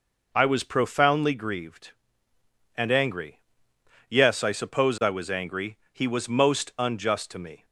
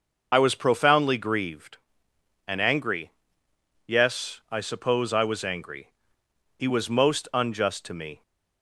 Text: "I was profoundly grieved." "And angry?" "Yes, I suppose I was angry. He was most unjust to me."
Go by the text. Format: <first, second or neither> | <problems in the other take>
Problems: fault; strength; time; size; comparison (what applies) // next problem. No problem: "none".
first | loses the start of "I"; at 0.3 s; 55 ms